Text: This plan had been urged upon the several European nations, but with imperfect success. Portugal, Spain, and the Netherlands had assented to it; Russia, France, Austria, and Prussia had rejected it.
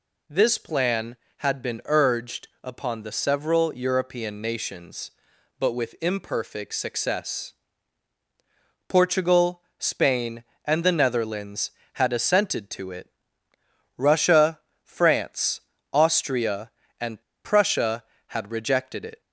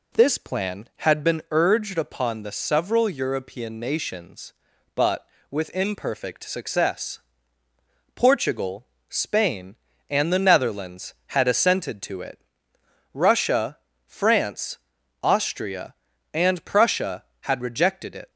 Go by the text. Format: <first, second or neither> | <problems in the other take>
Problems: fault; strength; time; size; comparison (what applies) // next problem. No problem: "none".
second | pauses between "and" and "Prussia"; slight; at 17.2 s; 0.24 s long